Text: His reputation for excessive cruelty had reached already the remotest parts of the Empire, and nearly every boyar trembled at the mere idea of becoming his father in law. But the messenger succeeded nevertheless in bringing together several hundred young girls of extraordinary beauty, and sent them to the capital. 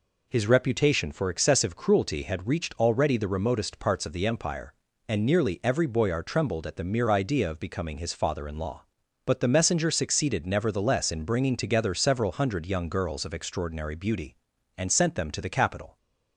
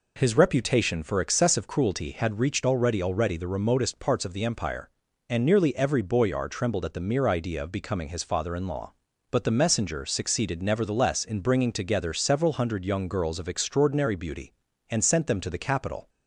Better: first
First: none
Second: says "already" twice; at 3.0 s

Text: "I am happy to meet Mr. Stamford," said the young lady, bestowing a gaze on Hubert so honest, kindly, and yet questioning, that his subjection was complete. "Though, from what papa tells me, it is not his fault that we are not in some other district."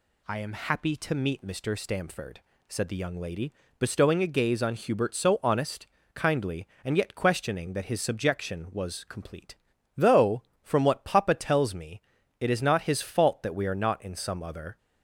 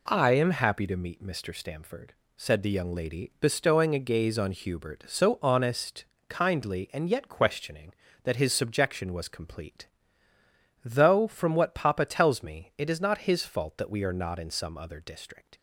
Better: second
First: stops before "district"; at 14.7 s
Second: none

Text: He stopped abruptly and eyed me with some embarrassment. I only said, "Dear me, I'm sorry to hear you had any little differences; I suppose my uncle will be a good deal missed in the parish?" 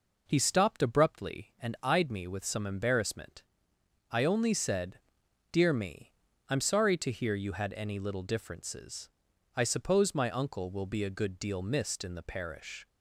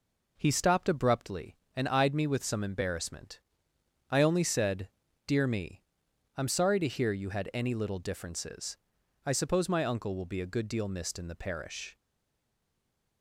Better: first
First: none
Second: stays silent after the last word; noticeable; from 11.9 s on; 1.3 s long

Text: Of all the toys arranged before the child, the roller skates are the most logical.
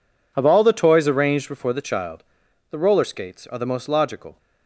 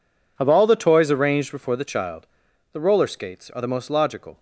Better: neither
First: none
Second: none

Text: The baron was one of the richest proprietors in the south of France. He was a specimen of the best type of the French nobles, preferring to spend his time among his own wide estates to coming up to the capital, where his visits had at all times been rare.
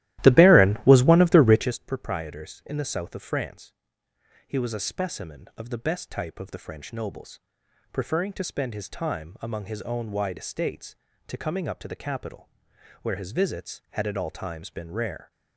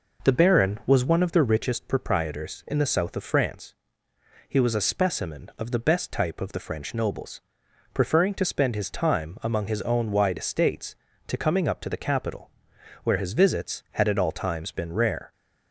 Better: second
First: starts louder than the rest; strong; until 1.8 s; 15 dB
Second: none

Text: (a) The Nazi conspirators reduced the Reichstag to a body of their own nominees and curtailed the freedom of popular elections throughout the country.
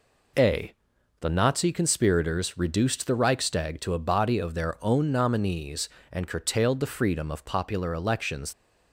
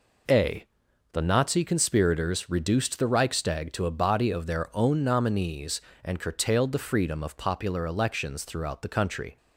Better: second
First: stops before "throughout the country"; at 8.5 s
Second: none

